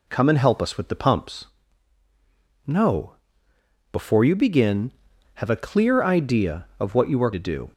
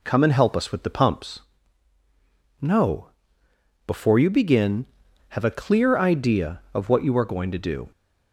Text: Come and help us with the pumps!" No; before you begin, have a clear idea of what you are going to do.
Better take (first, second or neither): second